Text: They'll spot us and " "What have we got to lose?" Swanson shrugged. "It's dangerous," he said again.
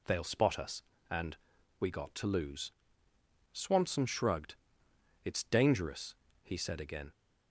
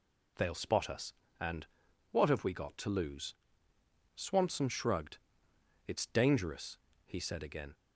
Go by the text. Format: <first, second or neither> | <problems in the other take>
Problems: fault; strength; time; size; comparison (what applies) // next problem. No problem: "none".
second | skips "What have"; at 1.8 s